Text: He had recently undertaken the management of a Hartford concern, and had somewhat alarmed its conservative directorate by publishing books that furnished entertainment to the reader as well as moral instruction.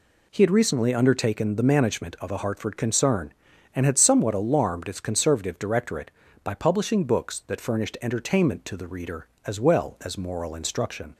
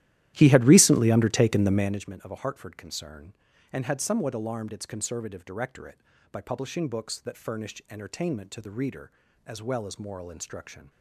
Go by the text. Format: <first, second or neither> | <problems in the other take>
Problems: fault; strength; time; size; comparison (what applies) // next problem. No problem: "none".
first | starts louder than the rest; strong; until 2.1 s; 13.5 dB